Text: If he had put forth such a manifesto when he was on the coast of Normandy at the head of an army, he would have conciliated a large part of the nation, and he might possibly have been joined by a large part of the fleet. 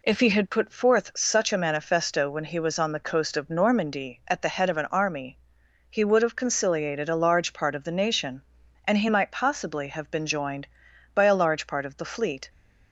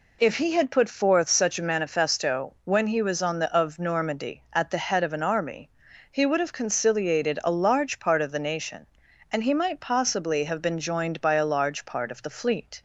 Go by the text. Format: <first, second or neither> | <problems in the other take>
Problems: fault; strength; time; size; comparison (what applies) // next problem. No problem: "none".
first | skips "coast"; at 3.5 s